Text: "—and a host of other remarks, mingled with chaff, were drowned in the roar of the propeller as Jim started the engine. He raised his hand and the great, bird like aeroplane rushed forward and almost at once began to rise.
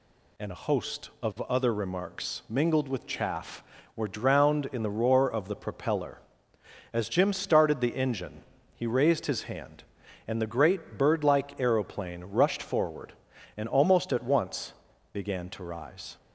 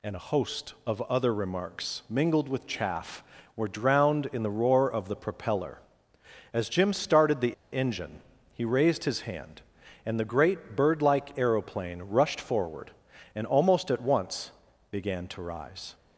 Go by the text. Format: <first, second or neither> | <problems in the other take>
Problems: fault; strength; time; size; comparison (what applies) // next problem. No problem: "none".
first | pauses between "the" and "engine"; slight; at 7.5 s; 0.18 s long // pauses between "once" and "began"; at 14.5 s; 0.40 s long; also in the first